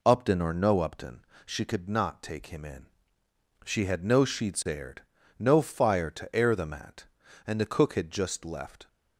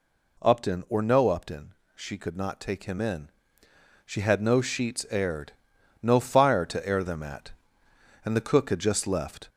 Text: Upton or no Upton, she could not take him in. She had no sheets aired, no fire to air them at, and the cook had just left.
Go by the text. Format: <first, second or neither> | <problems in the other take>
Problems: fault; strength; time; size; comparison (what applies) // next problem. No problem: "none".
first | gets louder; throughout; 4 dB